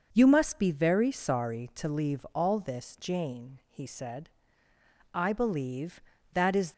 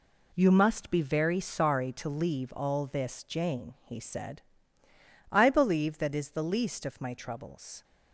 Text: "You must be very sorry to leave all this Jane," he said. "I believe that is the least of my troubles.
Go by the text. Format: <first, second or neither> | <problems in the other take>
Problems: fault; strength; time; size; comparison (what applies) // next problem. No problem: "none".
second | stops before "the least of my troubles"; at 6.7 s